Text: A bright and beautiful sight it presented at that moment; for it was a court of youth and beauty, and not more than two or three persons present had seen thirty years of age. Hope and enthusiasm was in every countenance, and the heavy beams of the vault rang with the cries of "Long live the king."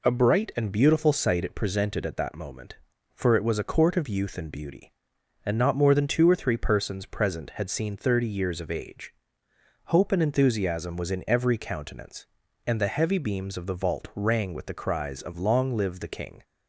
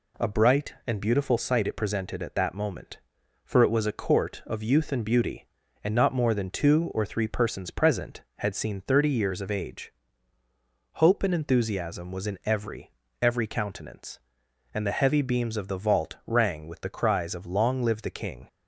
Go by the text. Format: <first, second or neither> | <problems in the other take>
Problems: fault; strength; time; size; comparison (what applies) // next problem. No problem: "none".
first | says "every" twice; at 13.2 s